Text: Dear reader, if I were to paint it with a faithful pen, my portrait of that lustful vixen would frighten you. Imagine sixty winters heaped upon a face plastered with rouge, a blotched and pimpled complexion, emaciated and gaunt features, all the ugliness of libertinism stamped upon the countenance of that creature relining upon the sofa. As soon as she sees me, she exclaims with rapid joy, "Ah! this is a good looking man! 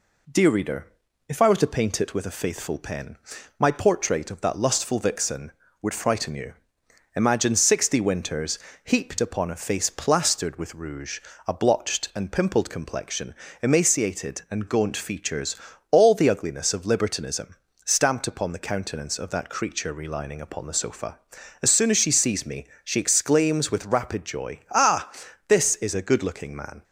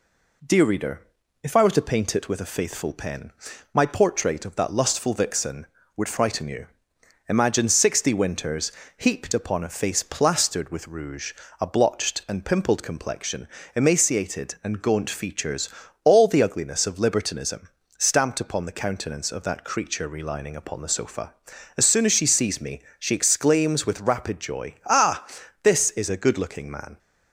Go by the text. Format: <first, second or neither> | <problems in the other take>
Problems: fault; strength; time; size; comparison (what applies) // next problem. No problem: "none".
neither | pauses between "winters" and "heaped"; slight; the same in both // pauses between "libertinism" and "stamped"; slight; the same in both